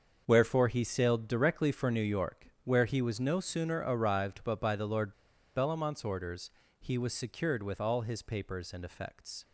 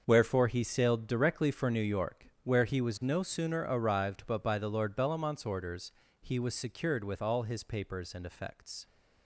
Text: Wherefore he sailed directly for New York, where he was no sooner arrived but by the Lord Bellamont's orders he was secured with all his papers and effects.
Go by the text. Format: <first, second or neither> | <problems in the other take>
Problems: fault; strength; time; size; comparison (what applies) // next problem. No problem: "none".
second | starts louder than the rest; until 1.2 s; 6.5 dB; also in the second // pauses between "Lord" and "Bellamont's"; at 5.1 s; 0.42 s long // pauses between "orders" and "he"; slight; at 6.5 s; 0.30 s long; slight in the second